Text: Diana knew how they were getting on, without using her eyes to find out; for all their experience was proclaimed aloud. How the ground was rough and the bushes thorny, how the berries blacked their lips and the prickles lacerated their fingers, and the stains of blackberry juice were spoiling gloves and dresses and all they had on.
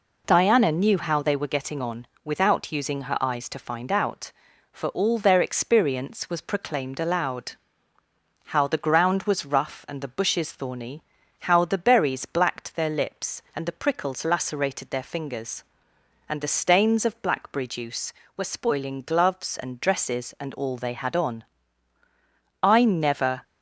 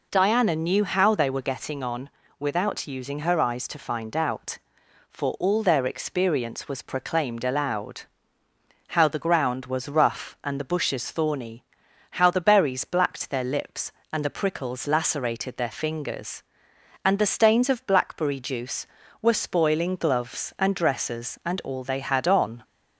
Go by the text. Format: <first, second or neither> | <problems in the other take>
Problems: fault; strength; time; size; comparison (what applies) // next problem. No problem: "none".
second | goes on to say "I never"; noticeable; from 22.6 s on; 0.80 s long